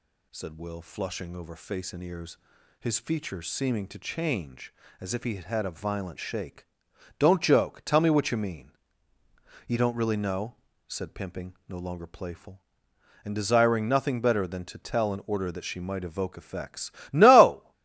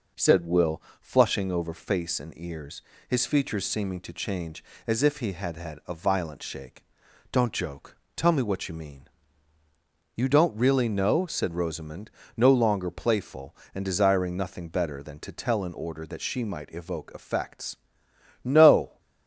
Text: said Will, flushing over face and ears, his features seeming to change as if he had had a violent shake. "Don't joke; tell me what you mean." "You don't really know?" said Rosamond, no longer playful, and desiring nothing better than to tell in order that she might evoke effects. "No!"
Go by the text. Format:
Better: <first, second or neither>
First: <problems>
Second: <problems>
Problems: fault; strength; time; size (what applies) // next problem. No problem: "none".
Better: second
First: says "Pimping" for "Rosamond"; at 11.1 s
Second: none